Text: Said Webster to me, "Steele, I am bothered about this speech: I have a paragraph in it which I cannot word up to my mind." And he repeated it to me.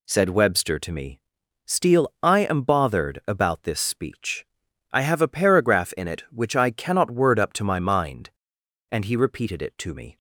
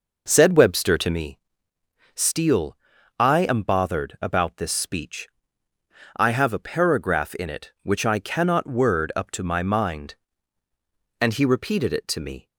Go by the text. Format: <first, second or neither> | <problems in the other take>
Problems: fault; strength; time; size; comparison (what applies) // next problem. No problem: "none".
first | starts louder than the rest; noticeable; until 1.3 s; 5.5 dB